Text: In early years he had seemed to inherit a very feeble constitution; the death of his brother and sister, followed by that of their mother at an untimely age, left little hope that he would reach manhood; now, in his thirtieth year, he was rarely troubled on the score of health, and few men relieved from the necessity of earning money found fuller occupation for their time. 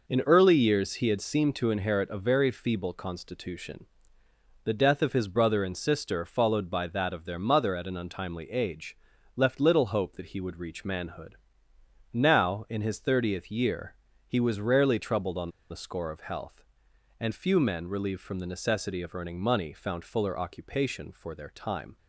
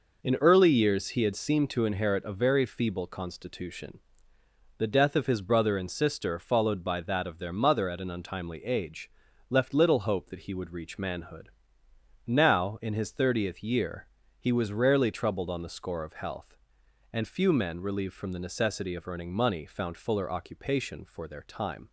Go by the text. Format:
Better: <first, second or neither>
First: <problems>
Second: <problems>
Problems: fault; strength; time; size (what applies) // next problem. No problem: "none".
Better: second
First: pauses between "on" and "the"; slight; at 15.4 s; 0.22 s long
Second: none